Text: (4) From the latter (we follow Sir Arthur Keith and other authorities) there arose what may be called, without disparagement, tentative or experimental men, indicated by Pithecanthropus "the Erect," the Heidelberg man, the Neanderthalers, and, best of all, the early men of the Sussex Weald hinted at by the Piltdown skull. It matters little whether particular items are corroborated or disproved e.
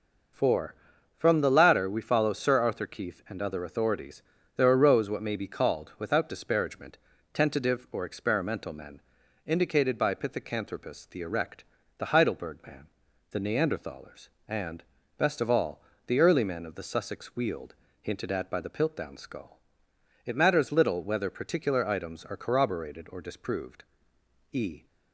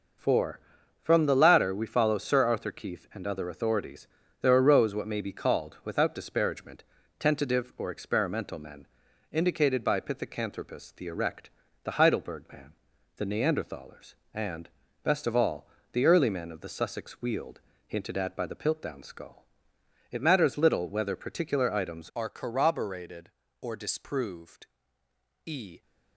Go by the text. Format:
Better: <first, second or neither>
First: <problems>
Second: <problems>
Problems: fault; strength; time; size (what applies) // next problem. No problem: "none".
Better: first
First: pauses between "Weald" and "hinted"; slight; at 17.7 s; 0.26 s long // pauses between "disproved" and "e"; noticeable; at 23.8 s; 0.68 s long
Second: pauses between "Weald" and "hinted"; slight; at 17.6 s; 0.26 s long // changes voice at "are"; from 22.1 s on; 3.7 s long // pauses between "disproved" and "e"; noticeable; at 24.6 s; 0.80 s long